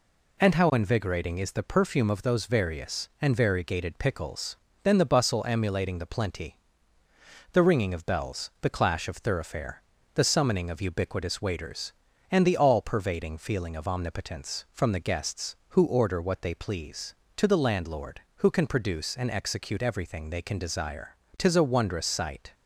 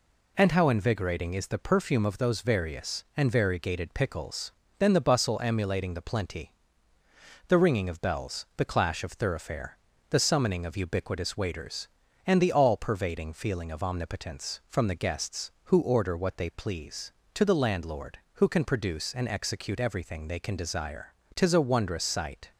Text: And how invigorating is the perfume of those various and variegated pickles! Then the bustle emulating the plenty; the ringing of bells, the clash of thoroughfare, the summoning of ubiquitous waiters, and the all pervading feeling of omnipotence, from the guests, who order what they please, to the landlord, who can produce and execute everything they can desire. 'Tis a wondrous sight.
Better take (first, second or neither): neither